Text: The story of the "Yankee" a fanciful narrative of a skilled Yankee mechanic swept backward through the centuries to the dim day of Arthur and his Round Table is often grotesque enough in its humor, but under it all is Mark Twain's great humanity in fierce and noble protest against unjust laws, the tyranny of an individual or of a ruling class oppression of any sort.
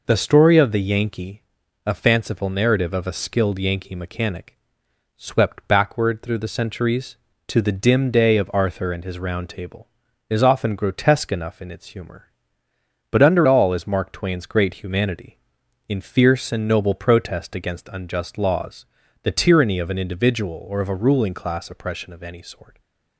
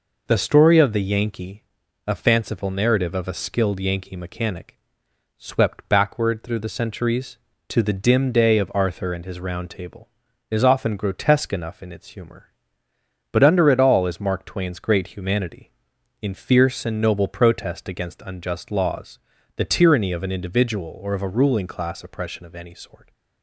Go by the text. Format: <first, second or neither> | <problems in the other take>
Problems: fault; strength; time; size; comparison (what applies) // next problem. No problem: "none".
second | pauses between "Yankee" and "a"; at 1.4 s; 0.42 s long; also in the second // pauses between "mechanic" and "swept"; noticeable; at 4.5 s; 0.60 s long; noticeable in the second // skips "it"; at 13.4 s